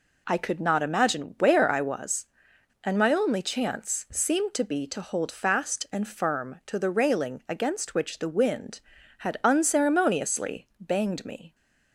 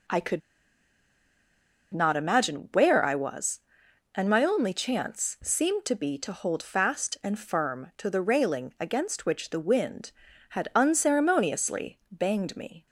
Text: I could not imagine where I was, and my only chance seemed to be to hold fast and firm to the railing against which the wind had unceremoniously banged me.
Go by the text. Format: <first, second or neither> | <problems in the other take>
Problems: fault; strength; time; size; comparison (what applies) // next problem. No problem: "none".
first | pauses between "could" and "not"; strong; at 0.4 s; 1.5 s long